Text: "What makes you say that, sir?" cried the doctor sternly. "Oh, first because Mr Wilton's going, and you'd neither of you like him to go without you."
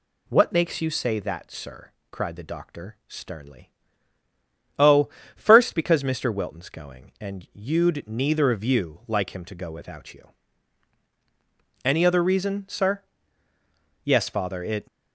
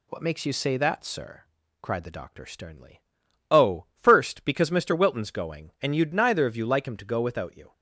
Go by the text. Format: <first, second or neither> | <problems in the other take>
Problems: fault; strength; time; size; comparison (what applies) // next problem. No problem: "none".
second | goes on to say "Any other reason sir Yes father It"; strong; from 11.8 s on; 3.0 s long